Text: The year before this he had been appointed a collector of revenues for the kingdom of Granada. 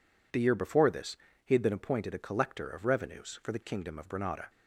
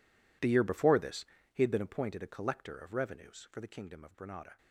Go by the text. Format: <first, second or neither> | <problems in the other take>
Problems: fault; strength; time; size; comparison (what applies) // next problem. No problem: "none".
first | gets quieter; strong; throughout; 17.5 dB // pauses between "this" and "he"; slight; at 1.2 s; 0.26 s long; slight in the first